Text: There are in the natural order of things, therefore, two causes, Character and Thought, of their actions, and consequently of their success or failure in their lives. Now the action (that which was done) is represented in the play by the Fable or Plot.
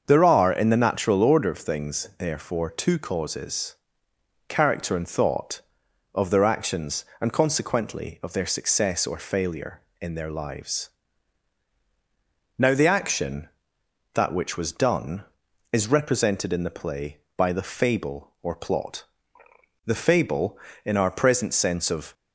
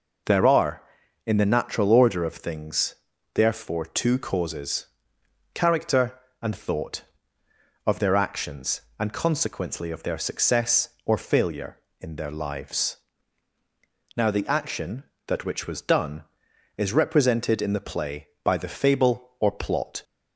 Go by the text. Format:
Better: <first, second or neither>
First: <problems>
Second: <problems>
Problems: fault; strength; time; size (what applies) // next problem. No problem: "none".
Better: second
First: starts louder than the rest; until 1.0 s; 6.5 dB // goes on to say "The Fable in our present sense of"; strong; from 19.8 s on; 2.2 s long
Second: none